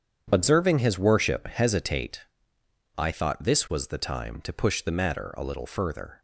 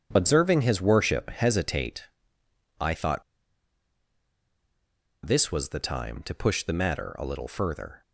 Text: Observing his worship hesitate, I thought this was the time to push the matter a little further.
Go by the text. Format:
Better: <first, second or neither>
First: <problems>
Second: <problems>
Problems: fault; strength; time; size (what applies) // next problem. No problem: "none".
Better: first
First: starts louder than the rest; strong; until 1.3 s; 8.5 dB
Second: starts louder than the rest; strong; until 1.1 s; 8.5 dB // pauses between "thought" and "this"; strong; at 3.2 s; 2.0 s long